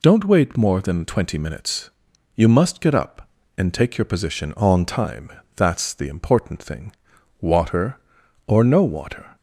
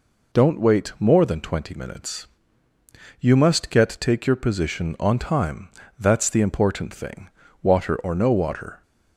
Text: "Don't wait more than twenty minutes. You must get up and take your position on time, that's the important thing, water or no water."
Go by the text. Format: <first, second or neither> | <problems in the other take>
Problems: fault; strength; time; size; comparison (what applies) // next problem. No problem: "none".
first | skips "up and"; at 3.9 s